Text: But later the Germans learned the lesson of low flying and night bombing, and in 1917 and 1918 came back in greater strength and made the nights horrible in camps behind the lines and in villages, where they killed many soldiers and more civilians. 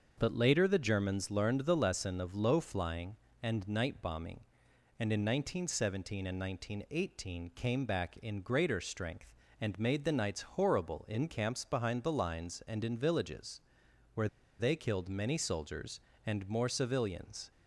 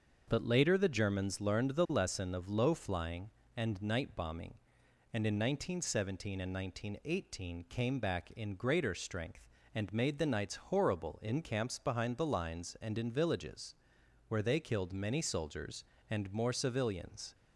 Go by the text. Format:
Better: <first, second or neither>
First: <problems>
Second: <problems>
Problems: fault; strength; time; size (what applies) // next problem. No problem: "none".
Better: second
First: starts louder than the rest; until 1.1 s; 6.5 dB // pauses between "where" and "they"; slight; at 14.2 s; 0.32 s long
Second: starts louder than the rest; until 1.2 s; 6.5 dB